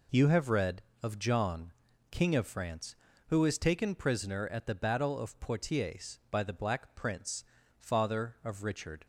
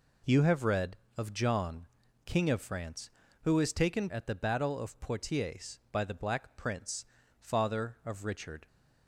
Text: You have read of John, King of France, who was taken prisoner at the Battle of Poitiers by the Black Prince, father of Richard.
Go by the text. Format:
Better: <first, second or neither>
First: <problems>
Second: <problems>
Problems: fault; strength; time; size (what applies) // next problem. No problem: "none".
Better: first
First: none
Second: skips "prisoner"; at 4.0 s